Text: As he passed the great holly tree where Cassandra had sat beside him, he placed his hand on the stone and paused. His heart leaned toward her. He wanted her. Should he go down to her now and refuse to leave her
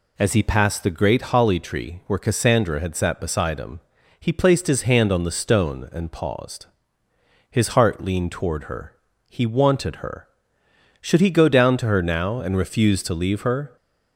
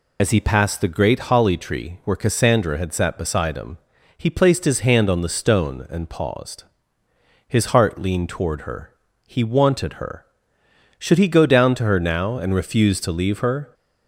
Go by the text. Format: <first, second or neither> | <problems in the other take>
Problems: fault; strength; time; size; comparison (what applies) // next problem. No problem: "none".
first | loses the start of "As"; at 0.1 s; 45 ms